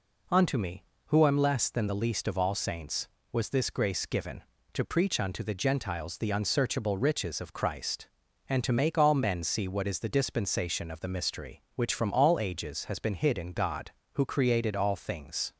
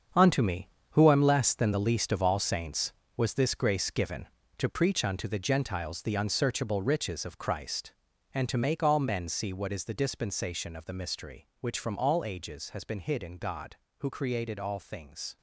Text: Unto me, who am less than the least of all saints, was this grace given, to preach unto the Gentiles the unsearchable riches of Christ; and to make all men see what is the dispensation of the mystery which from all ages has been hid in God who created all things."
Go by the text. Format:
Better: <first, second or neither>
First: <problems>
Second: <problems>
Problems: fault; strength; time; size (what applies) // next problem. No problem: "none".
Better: first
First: none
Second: gets quieter; strong; throughout; 10 dB